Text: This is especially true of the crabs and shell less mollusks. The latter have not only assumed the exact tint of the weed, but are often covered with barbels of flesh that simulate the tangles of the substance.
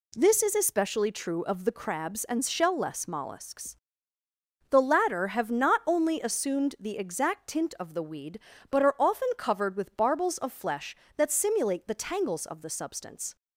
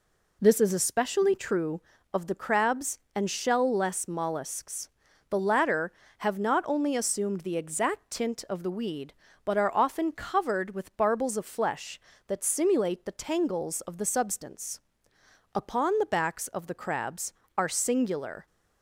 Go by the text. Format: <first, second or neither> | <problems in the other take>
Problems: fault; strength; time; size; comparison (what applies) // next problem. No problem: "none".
first | goes on to say "Upon the backs of the crabs are singular"; strong; from 15.5 s on; 2.9 s long